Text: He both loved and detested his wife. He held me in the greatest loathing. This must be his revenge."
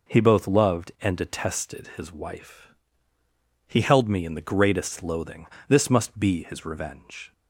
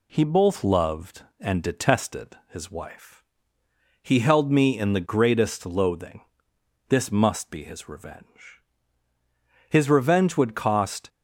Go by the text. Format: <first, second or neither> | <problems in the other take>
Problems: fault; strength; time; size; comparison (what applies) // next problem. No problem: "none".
first | goes on to say "His revenge would cost"; from 9.7 s on; 1.3 s long